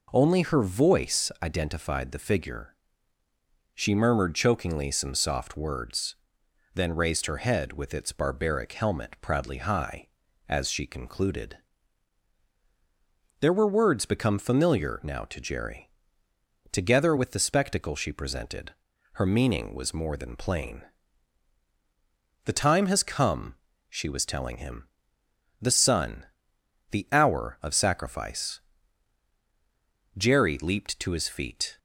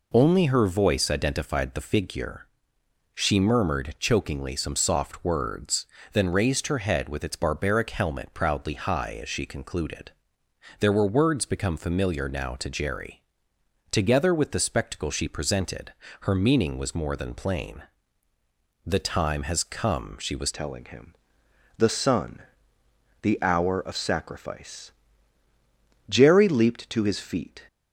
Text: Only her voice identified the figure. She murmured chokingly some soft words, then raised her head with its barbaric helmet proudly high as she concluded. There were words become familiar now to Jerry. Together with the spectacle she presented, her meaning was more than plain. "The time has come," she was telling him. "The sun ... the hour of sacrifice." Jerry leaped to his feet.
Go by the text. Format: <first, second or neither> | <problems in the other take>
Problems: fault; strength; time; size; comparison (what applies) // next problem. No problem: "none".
first | changes voice at "telling"; from 20.5 s on; 7.1 s long